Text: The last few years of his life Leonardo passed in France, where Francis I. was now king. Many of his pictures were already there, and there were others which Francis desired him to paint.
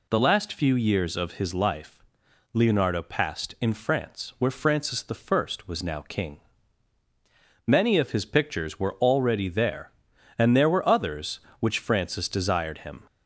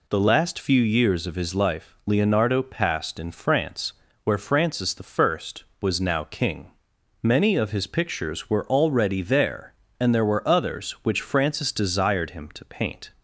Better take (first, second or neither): second